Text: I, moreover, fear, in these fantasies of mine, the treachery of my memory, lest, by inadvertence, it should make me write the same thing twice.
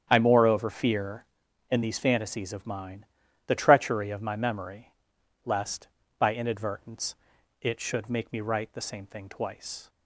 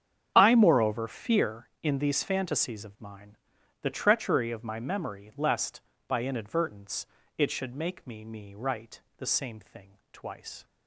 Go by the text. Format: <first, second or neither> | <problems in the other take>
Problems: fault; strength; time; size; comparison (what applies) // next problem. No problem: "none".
first | starts louder than the rest; strong; until 1.3 s; 8.5 dB; strong in the first // says "me" twice; at 8.2 s // pauses between "write" and "the"; slight; at 9.0 s; 0.18 s long